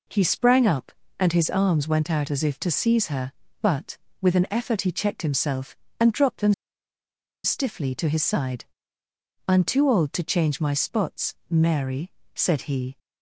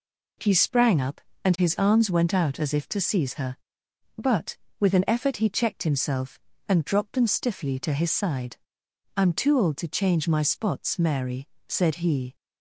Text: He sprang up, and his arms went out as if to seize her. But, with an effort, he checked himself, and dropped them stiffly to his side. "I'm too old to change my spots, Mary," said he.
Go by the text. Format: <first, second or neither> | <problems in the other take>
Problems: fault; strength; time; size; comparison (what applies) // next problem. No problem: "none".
second | pauses between "them" and "stiffly"; noticeable; at 6.5 s; 0.90 s long